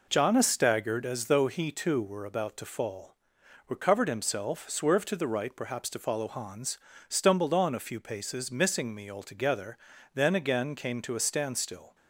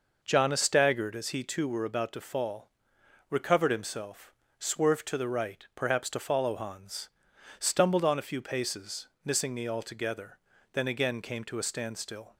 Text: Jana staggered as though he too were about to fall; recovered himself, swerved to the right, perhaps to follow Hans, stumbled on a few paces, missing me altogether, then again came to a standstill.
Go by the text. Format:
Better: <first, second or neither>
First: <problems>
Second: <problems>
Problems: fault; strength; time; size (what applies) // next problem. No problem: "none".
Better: first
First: none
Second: skips "though"; at 1.2 s